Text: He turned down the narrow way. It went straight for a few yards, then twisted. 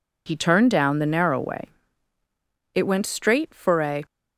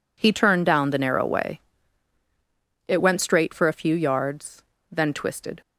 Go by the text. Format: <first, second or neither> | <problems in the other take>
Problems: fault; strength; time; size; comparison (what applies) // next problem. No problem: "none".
second | stops before "few yards then twisted"; at 4.0 s